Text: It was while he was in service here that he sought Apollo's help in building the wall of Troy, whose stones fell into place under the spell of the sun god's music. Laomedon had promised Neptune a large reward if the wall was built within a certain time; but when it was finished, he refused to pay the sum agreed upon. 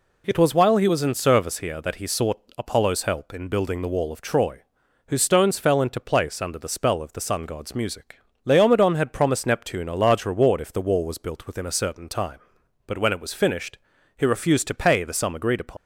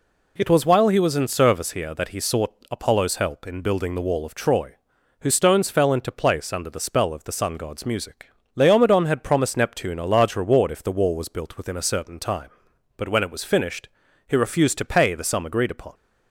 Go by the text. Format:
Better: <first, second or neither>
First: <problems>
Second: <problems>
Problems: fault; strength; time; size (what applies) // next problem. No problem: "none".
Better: second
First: pauses between "sought" and "Apollo's"; slight; at 2.3 s; 0.18 s long // leaves "upon" unfinished; at 15.7 s; 65 ms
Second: pauses between "sought" and "Apollo's"; slight; at 2.5 s; 0.18 s long